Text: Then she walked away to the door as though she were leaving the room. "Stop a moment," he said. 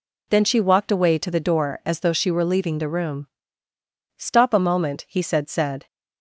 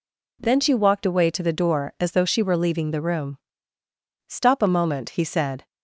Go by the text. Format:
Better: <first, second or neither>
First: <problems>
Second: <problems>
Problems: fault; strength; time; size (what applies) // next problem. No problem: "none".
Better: second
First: says "said" twice; at 5.4 s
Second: none